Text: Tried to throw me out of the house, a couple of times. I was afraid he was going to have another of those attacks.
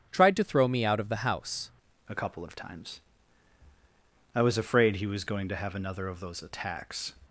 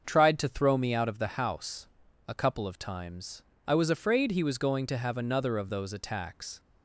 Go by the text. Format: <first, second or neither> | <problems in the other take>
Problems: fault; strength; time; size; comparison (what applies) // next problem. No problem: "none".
second | starts louder than the rest; strong; until 1.1 s; 11 dB; also in the second // changes voice at "a"; from 2.0 s on; 5.1 s long